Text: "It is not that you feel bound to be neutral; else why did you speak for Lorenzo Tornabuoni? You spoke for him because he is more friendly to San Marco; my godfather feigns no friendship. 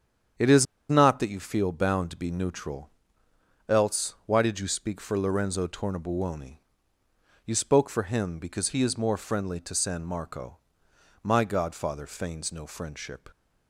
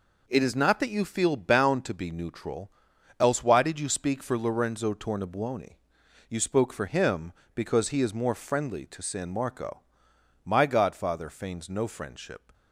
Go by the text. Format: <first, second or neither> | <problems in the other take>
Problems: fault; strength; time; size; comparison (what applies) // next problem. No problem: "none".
second | starts louder than the rest; strong; until 1.6 s; 8 dB // pauses between "is" and "not"; slight; at 0.6 s; 0.25 s long